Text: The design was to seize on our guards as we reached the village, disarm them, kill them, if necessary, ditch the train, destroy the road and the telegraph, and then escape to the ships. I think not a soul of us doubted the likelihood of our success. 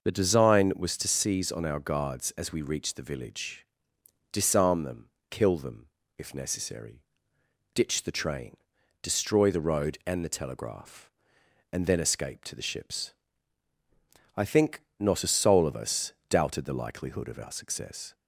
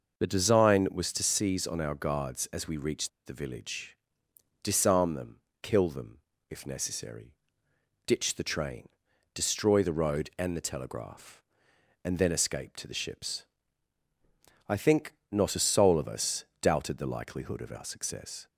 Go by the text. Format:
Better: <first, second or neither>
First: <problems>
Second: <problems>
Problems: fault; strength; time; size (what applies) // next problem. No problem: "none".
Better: first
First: pauses between "think" and "not"; slight; at 14.7 s; 0.22 s long // pauses between "us" and "doubted"; slight; at 16.1 s; 0.16 s long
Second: pauses between "reached" and "the"; slight; at 3.0 s; 0.17 s long // pauses between "think" and "not"; slight; at 15.1 s; 0.22 s long // pauses between "us" and "doubted"; slight; at 16.4 s; 0.16 s long